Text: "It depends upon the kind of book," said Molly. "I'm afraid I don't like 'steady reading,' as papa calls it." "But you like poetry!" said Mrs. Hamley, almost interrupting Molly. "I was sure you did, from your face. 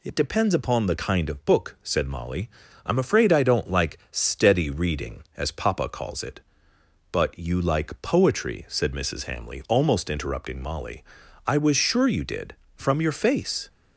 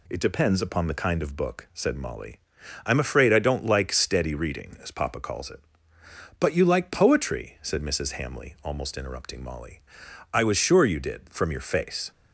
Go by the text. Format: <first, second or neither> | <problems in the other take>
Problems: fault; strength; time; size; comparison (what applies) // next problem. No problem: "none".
neither | none